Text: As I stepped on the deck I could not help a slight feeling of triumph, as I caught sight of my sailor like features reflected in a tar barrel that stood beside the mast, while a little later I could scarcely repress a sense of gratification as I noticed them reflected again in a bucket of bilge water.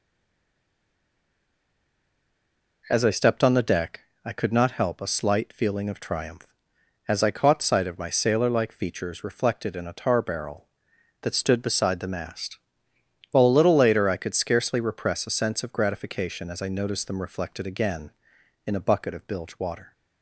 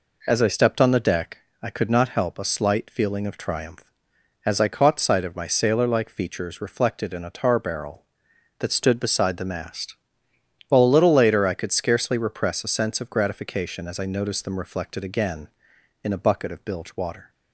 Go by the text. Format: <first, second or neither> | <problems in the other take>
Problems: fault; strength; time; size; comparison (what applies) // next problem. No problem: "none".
second | stays silent before the first word; strong; until 2.8 s; 2.8 s long // pauses between "deck" and "I"; slight; at 4.0 s; 0.26 s long; slight in the second